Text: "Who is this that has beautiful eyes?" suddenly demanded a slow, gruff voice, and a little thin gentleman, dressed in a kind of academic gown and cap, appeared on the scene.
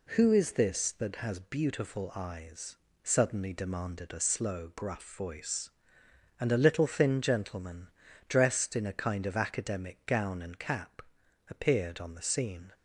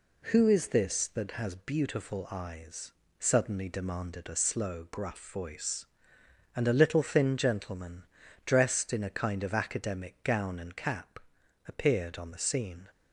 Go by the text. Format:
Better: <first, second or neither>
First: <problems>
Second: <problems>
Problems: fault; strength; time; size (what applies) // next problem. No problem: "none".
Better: neither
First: none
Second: none